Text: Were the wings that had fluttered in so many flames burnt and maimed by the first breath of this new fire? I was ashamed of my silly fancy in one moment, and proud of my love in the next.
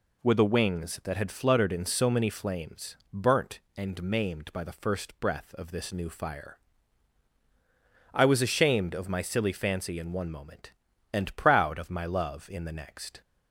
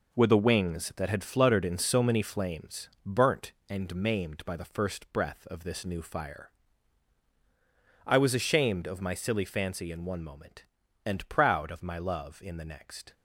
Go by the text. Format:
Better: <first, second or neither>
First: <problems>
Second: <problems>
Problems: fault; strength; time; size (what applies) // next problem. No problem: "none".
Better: first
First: pauses between "flames" and "burnt"; slight; at 2.9 s; 0.16 s long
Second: gets quieter; strong; throughout; 8 dB // pauses between "flames" and "burnt"; slight; at 2.8 s; 0.16 s long